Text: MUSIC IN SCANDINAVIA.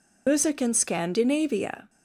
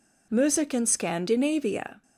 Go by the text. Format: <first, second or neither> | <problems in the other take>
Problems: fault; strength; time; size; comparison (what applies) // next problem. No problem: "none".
second | loses the start of "MUSIC"; at 0.2 s; 90 ms